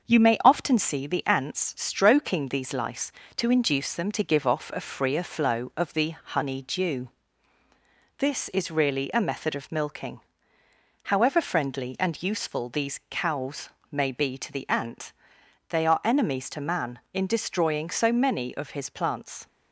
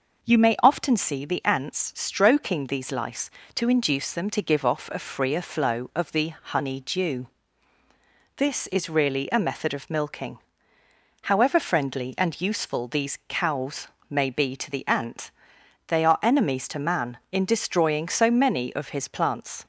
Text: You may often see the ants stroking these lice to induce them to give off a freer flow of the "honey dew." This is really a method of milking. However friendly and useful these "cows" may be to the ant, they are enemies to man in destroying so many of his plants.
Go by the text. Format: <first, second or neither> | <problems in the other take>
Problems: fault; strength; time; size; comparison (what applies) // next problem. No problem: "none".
second | gets quieter; slight; throughout; 2.5 dB // pauses between "cows" and "may"; slight; at 13.6 s; 0.24 s long; slight in the second